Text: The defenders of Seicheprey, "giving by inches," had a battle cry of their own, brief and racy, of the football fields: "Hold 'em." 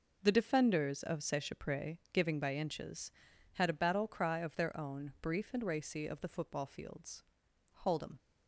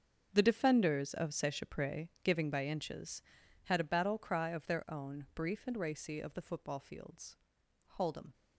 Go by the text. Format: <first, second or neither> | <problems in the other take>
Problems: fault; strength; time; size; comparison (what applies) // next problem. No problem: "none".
first | gets quieter; strong; throughout; 15.5 dB